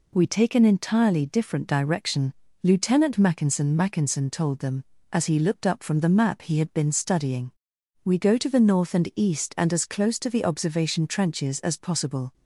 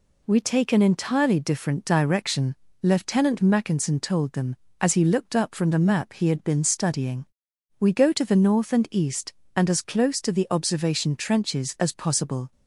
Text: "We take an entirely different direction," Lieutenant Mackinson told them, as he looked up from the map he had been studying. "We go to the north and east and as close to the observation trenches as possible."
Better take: second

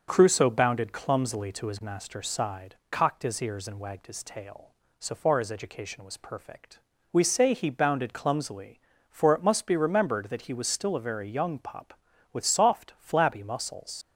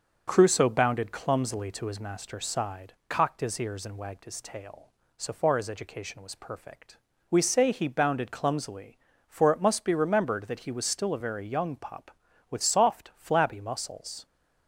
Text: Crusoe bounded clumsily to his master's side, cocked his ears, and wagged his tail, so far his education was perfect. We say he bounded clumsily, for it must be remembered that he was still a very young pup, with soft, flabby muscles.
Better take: second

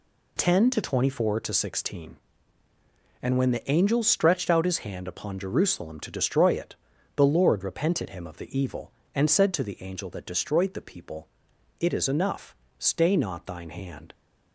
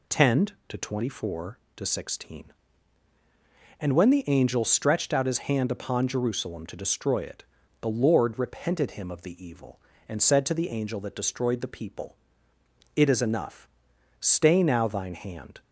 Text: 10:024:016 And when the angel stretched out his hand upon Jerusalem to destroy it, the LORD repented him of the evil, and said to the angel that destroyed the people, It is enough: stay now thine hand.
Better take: second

